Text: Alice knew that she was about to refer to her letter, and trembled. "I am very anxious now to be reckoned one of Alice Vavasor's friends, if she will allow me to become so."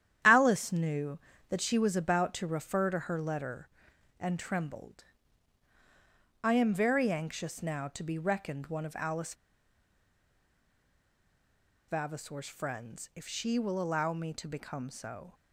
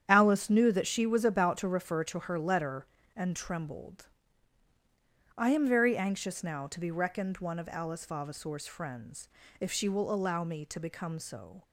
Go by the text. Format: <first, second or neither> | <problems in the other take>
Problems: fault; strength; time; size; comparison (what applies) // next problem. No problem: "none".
second | starts louder than the rest; strong; until 1.5 s; 10.5 dB; strong in the second // pauses between "Alice" and "Vavasor's"; strong; at 9.3 s; 2.5 s long